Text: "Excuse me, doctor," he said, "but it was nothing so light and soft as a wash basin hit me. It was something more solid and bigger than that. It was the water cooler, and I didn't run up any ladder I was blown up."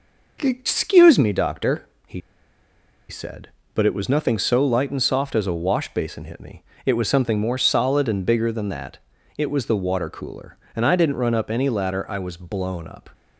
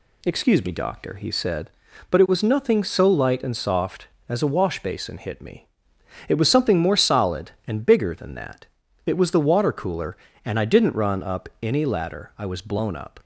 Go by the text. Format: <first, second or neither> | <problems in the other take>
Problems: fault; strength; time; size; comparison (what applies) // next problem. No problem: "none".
second | pauses between "he" and "said"; noticeable; at 2.2 s; 0.89 s long